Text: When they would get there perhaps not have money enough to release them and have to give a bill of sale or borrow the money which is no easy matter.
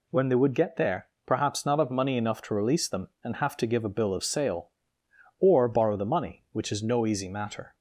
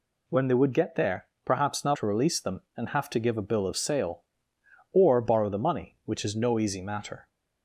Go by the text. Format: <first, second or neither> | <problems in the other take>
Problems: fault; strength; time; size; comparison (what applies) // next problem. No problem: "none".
first | pauses between "there" and "perhaps"; slight; at 1.2 s; 0.18 s long; slight in the first // skips "have money enough"; at 1.9 s